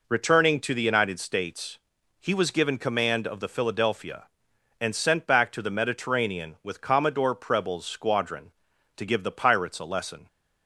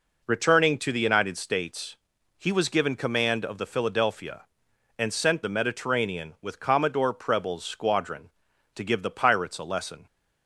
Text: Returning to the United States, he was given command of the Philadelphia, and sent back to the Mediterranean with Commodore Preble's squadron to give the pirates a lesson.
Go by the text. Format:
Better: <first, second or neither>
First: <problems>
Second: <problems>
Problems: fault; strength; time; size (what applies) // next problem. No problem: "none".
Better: first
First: none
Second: skips "back to"; at 5.4 s